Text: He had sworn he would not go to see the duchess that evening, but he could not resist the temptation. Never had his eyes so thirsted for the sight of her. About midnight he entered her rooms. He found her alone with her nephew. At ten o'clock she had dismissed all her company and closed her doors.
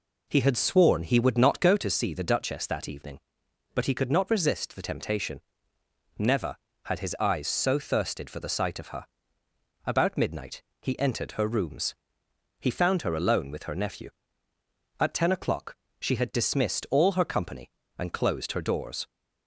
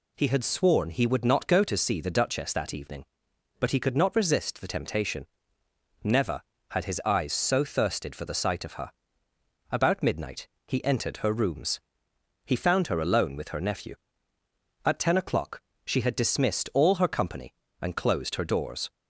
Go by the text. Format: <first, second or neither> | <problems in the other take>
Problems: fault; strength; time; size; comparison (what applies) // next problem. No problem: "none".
second | starts louder than the rest; until 1.8 s; 4 dB // pauses between "midnight" and "he"; slight; at 10.6 s; 0.20 s long; slight in the second // pauses between "o'clock" and "she"; slight; at 15.7 s; 0.24 s long; slight in the second